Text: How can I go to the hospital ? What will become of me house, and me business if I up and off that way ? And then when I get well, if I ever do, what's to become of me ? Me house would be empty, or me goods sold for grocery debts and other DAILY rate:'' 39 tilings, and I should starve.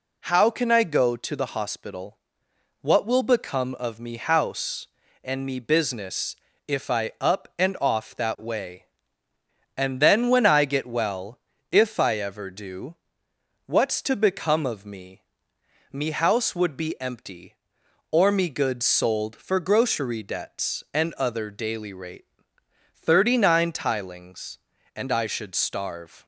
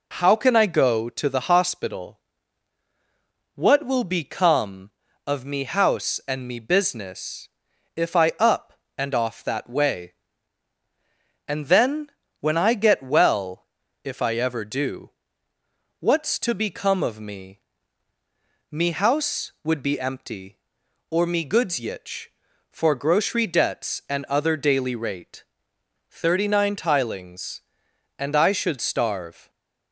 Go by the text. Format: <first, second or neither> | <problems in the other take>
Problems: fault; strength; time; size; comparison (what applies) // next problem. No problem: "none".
first | pauses between "business" and "if"; noticeable; at 7.4 s; 0.48 s long; slight in the first // pauses between "then" and "when"; slight; at 12.0 s; 0.30 s long // says "yitch" for "sold"; at 21.7 s